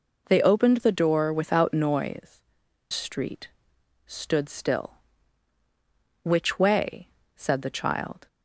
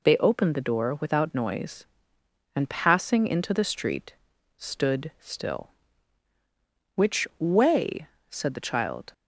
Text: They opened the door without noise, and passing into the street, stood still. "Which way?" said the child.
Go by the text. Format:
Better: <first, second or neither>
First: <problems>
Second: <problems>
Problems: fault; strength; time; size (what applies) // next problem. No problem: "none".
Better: second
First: skips "and passing into the"; at 2.6 s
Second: none